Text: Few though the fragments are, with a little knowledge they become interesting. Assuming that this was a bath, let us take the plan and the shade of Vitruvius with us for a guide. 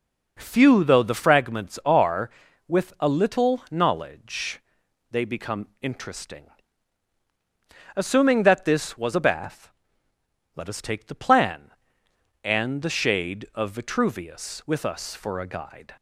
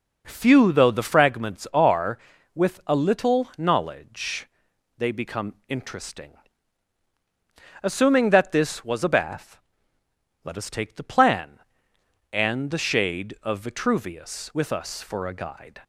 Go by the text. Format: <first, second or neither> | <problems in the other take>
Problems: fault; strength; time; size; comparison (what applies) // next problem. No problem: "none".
neither | pauses between "knowledge" and "they"; noticeable; the same in both